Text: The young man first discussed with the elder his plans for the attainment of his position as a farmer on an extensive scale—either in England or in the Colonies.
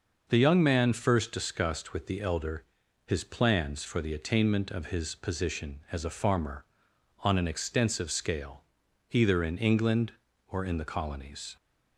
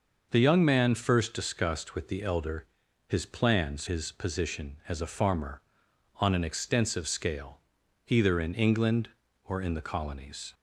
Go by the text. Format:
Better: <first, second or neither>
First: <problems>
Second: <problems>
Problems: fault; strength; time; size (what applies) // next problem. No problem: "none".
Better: first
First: pauses between "elder" and "his"; at 2.6 s; 0.40 s long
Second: pauses between "elder" and "his"; at 2.6 s; 0.40 s long // skips "for the attainment of"; at 3.8 s